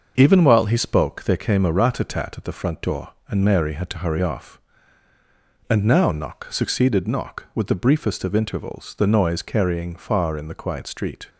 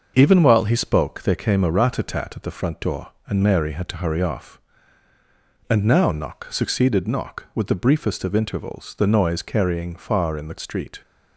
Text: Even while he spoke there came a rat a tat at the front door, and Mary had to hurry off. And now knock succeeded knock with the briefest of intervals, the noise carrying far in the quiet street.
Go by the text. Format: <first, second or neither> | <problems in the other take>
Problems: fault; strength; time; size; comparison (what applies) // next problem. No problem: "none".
first | starts louder than the rest; until 1.1 s; 6.5 dB; also in the first // skips "quiet"; at 10.5 s